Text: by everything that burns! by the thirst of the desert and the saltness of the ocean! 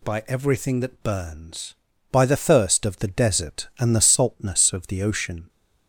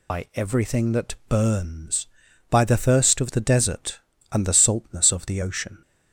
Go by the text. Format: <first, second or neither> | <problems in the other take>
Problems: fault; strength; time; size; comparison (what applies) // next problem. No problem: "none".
first | loses the start of "by"; at 0.0 s; 45 ms